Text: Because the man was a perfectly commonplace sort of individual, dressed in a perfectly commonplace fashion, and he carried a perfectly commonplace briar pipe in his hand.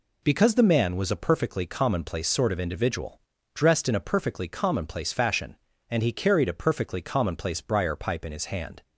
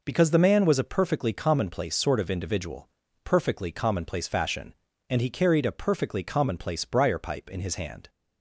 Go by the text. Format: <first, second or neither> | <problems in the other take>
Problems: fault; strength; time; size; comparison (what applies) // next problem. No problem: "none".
first | skips "dressed in a"; at 3.0 s